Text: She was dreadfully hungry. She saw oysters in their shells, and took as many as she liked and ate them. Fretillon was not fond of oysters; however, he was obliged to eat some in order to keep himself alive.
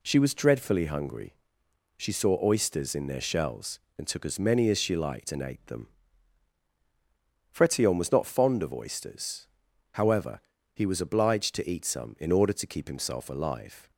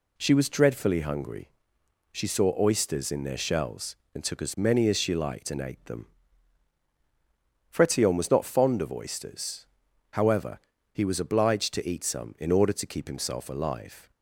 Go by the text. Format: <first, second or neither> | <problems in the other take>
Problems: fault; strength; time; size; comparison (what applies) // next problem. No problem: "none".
neither | none